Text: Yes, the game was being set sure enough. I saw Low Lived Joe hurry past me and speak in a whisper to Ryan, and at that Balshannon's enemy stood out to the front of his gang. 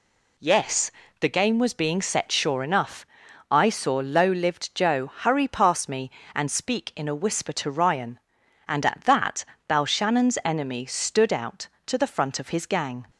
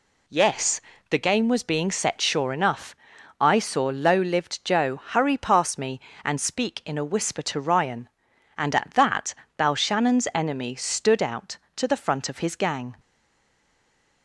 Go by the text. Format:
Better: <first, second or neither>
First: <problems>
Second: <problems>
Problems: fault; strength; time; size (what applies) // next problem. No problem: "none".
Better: first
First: pauses between "that" and "Balshannon's"; slight; at 9.4 s; 0.24 s long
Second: pauses between "that" and "Balshannon's"; slight; at 9.3 s; 0.24 s long // stays silent after the last word; noticeable; from 12.9 s on; 1.3 s long